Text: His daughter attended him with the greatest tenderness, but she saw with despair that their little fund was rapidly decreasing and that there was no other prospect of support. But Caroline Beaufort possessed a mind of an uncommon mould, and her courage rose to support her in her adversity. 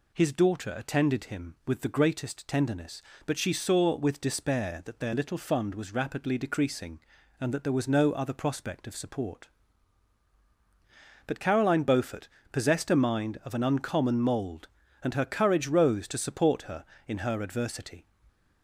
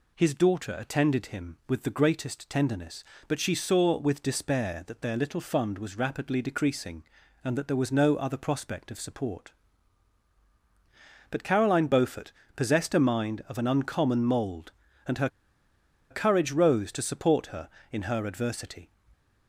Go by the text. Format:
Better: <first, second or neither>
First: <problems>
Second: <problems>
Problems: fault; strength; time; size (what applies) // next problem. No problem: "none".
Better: first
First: pauses between "Beaufort" and "possessed"; slight; at 12.2 s; 0.22 s long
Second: pauses between "Beaufort" and "possessed"; slight; at 12.3 s; 0.22 s long // pauses between "her" and "courage"; noticeable; at 15.2 s; 0.82 s long